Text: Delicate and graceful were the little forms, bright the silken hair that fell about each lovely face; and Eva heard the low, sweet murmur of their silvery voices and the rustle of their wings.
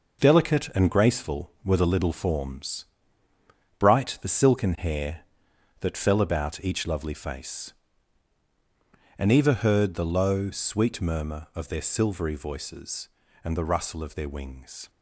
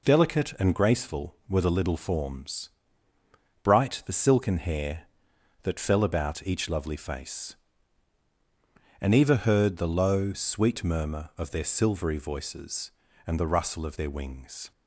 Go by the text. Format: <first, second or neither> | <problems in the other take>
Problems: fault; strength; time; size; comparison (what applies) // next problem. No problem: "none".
second | gets quieter; strong; throughout; 8 dB